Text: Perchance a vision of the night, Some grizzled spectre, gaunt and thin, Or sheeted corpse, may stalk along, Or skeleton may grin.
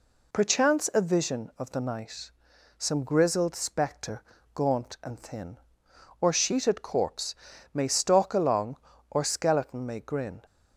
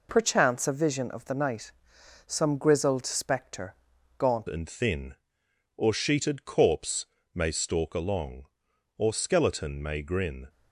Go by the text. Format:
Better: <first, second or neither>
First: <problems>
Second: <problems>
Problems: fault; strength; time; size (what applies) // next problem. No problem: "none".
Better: first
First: none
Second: changes voice at "and"; from 4.4 s on; 6.0 s long